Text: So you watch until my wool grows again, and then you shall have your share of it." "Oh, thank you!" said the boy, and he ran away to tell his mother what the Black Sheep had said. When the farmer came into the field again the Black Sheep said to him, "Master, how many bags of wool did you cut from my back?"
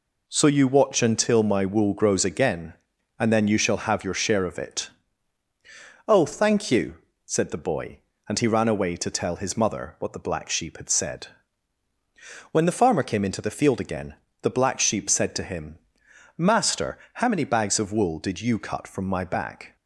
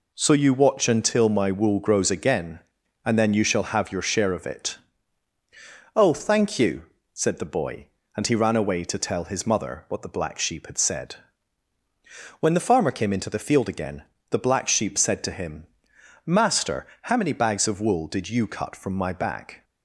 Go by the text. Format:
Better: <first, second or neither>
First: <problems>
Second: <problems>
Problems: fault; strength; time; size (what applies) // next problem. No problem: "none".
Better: neither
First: pauses between "again" and "the"; slight; at 14.1 s; 0.28 s long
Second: pauses between "again" and "the"; slight; at 14.0 s; 0.28 s long